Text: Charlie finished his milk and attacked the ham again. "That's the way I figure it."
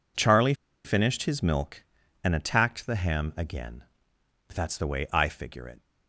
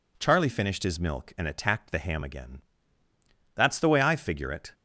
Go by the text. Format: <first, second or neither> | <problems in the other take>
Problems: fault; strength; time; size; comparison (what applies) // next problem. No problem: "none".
second | pauses between "Charlie" and "finished"; slight; at 0.5 s; 0.31 s long